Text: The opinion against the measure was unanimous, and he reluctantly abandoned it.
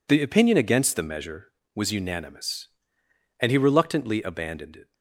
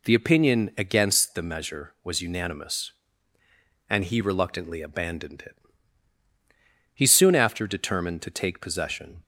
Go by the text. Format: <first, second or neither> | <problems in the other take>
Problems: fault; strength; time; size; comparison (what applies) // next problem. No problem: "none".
first | goes on to say "He soon after determined to take possession"; strong; from 6.9 s on; 2.2 s long